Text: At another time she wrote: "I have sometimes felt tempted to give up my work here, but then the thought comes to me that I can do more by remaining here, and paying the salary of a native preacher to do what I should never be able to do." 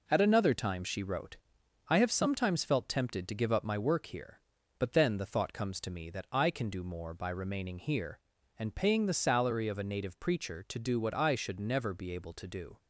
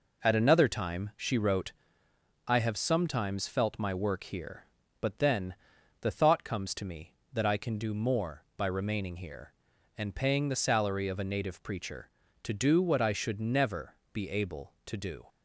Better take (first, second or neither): first